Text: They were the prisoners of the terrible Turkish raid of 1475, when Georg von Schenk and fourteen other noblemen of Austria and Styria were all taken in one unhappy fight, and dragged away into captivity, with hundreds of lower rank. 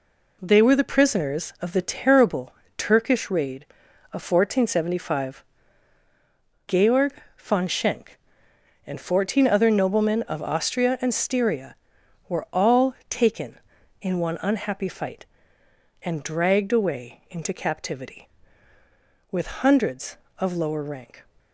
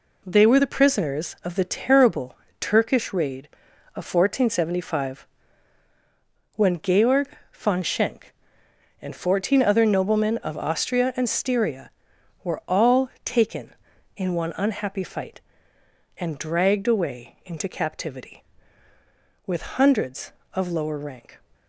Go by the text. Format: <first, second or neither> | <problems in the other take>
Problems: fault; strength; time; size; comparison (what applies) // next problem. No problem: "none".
second | pauses between "terrible" and "Turkish"; slight; at 2.5 s; 0.24 s long; slight in the second // skips "when"; at 6.0 s // pauses between "Georg" and "von"; slight; at 7.1 s; 0.24 s long; slight in the second